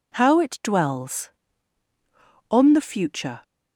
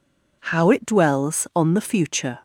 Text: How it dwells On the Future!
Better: neither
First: none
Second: none

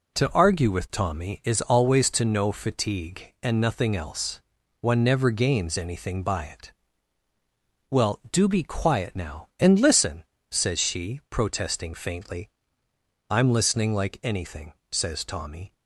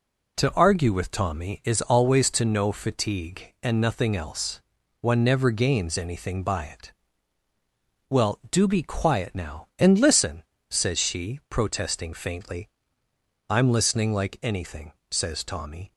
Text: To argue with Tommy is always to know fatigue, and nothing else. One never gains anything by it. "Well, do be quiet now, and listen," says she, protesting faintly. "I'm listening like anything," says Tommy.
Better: neither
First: none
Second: none

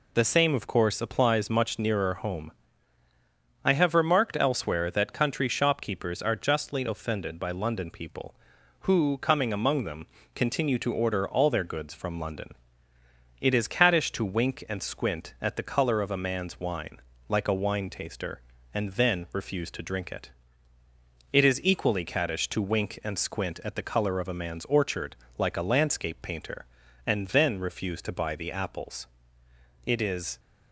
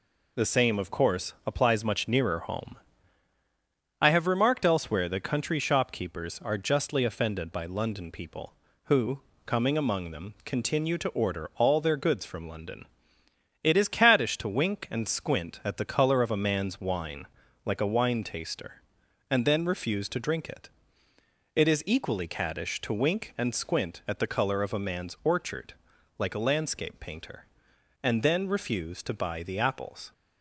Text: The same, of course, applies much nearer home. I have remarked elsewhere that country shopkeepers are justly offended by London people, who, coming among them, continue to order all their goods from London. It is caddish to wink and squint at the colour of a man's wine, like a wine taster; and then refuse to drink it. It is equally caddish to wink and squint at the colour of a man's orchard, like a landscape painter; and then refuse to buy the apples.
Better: second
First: goes on to say "It is"; from 29.8 s on; 0.54 s long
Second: none

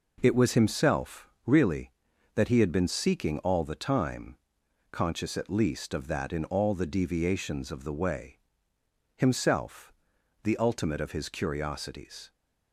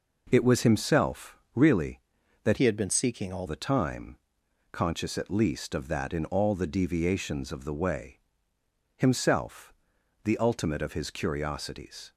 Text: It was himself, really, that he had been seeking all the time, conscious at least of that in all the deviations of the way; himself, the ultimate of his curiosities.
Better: first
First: none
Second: changes voice from "he" to "all"; from 2.5 to 3.4 s; 0.9 s long

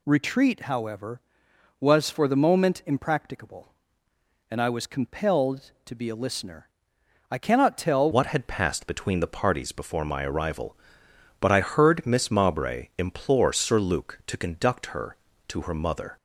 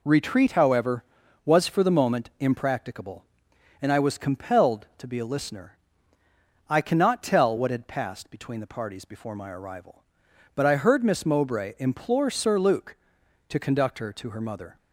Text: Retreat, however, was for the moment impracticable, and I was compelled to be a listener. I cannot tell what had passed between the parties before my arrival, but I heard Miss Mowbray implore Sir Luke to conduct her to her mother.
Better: second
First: changes voice at "what"; from 8.1 s on; 8.0 s long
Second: none

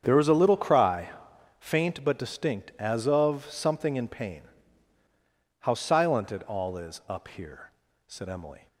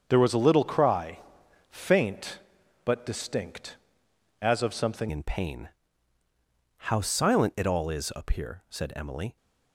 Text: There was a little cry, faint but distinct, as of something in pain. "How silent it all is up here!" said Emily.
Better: first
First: starts louder than the rest; strong; until 1.0 s; 7.5 dB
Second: starts louder than the rest; until 1.0 s; 7 dB // changes voice at "in"; from 5.0 s on; 4.3 s long

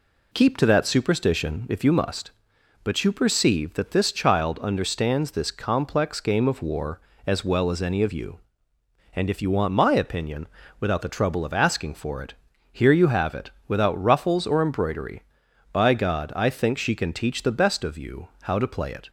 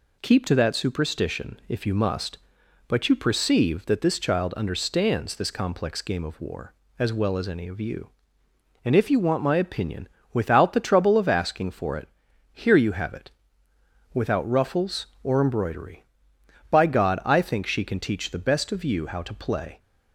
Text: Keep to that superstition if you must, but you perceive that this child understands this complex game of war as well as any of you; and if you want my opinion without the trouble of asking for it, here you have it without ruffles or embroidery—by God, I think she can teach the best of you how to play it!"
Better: first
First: pauses between "opinion" and "without"; slight; at 10.4 s; 0.32 s long // pauses between "it" and "without"; slight; at 13.5 s; 0.16 s long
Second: pauses between "opinion" and "without"; slight; at 10.0 s; 0.24 s long // pauses between "it" and "without"; noticeable; at 13.2 s; 0.84 s long // stops before "it"; at 19.7 s

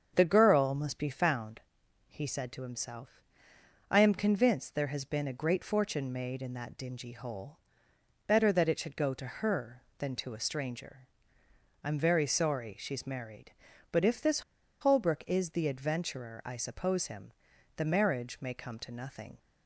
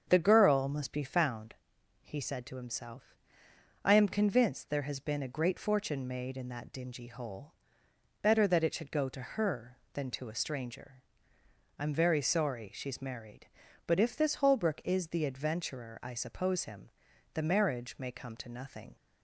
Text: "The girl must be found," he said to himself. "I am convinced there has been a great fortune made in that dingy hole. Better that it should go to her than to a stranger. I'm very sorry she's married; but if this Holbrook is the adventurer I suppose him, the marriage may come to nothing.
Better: second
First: starts louder than the rest; strong; until 1.1 s; 7 dB // pauses between "this" and "Holbrook"; at 14.4 s; 0.40 s long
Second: starts louder than the rest; strong; until 1.0 s; 7 dB

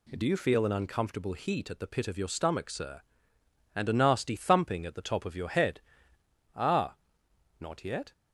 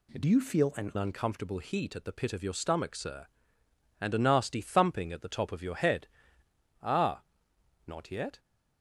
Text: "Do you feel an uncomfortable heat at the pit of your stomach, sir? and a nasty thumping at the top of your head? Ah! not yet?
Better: first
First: none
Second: changes voice from "you" to "an"; from 0.2 to 0.9 s; 0.7 s long

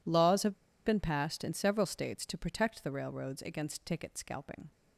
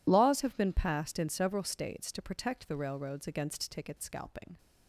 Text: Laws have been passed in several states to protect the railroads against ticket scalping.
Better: second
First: pauses between "have" and "been"; slight; at 0.5 s; 0.30 s long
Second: none

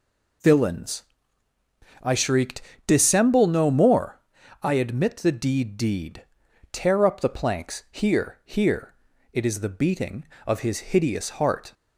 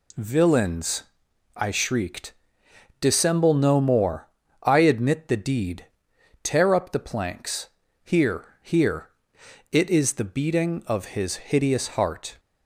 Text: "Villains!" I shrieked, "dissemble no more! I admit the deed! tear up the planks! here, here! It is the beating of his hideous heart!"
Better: second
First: says "deed" twice; at 5.7 s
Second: none

